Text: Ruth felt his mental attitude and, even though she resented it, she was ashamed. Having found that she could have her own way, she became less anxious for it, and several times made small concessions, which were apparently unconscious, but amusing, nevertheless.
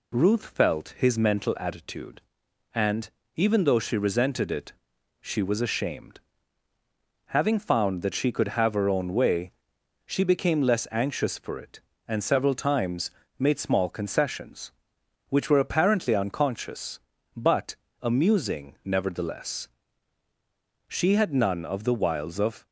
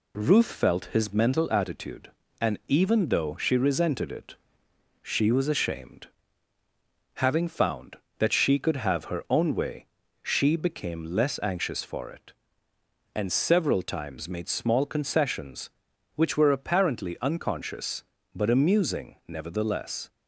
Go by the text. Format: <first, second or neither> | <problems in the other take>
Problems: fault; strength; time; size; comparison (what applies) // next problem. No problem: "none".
second | pauses between "times" and "made"; slight; at 13.1 s; 0.26 s long // pauses between "but" and "amusing"; slight; at 17.7 s; 0.26 s long // goes on to say "She had none of the wiles of"; strong; from 20.8 s on; 1.7 s long